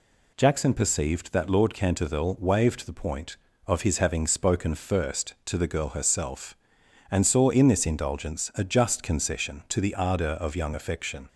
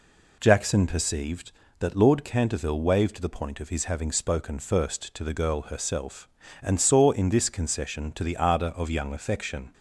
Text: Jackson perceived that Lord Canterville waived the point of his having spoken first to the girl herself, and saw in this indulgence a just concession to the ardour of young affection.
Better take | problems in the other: first | skips "indulgence a just"; at 7.4 s

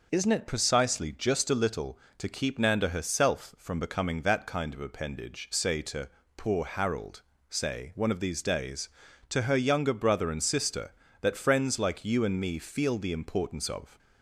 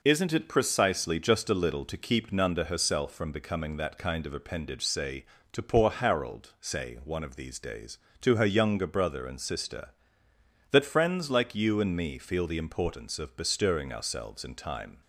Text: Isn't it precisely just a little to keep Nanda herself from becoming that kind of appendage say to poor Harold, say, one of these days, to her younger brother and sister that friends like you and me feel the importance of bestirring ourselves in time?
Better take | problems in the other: second | pauses between "to" and "poor"; slight; at 6.0 s; 0.30 s long // stops before "bestirring ourselves in time"; at 13.9 s

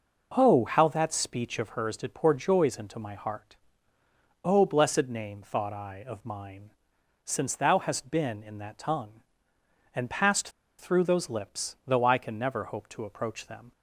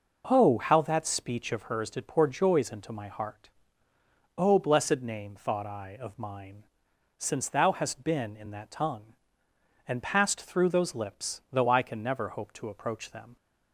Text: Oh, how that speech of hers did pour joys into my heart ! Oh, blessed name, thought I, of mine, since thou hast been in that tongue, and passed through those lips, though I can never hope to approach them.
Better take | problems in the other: second | pauses between "passed" and "through"; slight; at 10.4 s; 0.30 s long

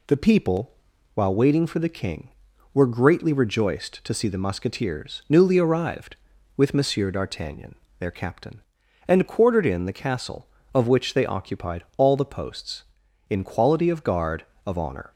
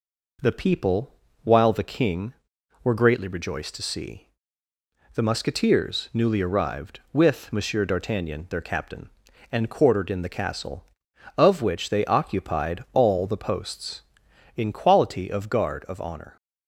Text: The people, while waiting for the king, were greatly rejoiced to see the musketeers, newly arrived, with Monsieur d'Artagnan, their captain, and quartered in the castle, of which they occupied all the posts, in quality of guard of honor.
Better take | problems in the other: first | skips "waiting for"; at 1.7 s // pauses between "see" and "the"; noticeable; at 4.2 s; 0.86 s long

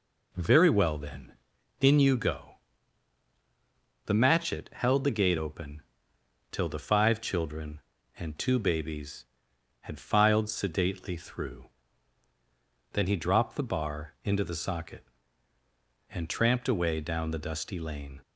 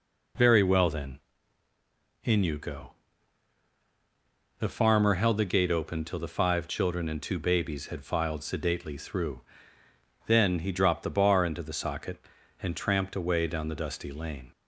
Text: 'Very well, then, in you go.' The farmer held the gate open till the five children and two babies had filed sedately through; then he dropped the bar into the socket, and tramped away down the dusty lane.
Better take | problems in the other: second | says "matchet" for "farmer"; at 4.1 s // pauses between "open" and "till"; noticeable; at 5.8 s; 0.70 s long

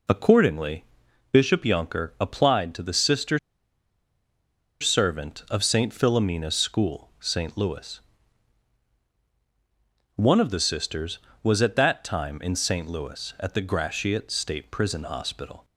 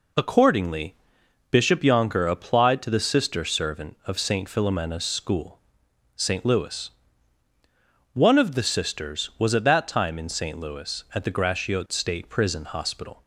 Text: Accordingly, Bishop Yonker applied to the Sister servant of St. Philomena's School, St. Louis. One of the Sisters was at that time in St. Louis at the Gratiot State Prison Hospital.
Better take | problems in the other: second | pauses between "Sister" and "servant"; strong; at 3.3 s; 1.4 s long

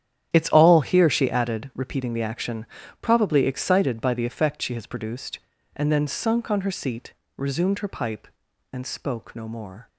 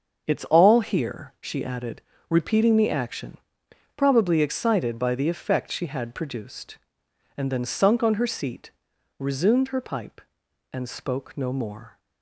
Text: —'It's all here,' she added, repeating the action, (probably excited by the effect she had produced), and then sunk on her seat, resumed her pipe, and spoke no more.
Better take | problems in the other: second | starts louder than the rest; strong; until 1.3 s; 10.5 dB; also in the second // says "has" for "had"; at 4.7 s

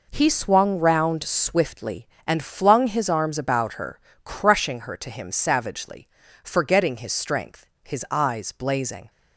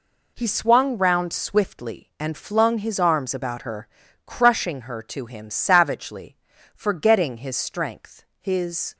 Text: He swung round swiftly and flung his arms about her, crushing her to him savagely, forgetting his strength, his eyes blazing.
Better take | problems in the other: first | stops before "eyes blazing"; at 8.9 s

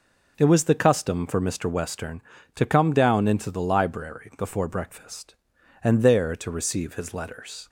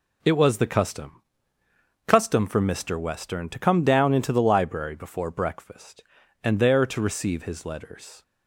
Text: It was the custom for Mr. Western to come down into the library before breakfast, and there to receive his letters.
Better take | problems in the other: first | says "custom" twice; at 2.0 s

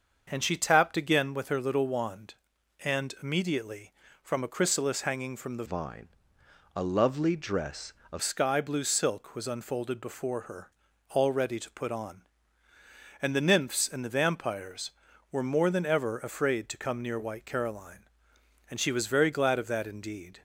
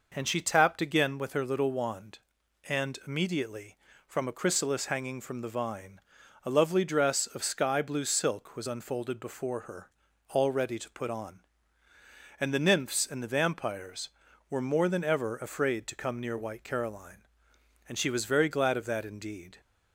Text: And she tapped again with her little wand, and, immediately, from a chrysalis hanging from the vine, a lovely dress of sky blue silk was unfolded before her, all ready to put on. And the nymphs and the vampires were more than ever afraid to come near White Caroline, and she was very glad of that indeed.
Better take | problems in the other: second | starts louder than the rest; until 1.3 s; 6.5 dB // changes voice from "vine" to "of"; from 5.6 to 8.2 s; 2.6 s long

